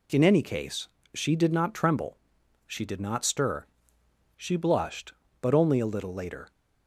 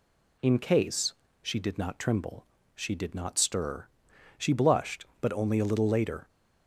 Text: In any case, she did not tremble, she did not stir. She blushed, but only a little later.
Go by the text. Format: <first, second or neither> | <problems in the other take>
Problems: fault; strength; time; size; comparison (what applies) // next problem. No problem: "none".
first | skips "any"; at 0.5 s